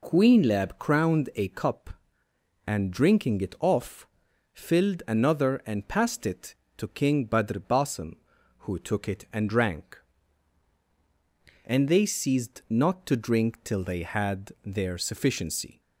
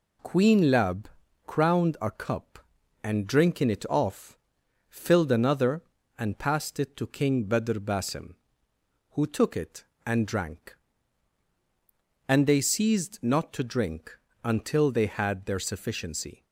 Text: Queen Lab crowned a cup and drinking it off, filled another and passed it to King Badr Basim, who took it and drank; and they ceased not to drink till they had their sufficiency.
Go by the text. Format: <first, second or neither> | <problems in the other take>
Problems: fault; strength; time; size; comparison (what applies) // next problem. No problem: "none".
first | pauses between "Lab" and "crowned"; at 1.0 s; 0.40 s long // says "until" for "till"; at 14.4 s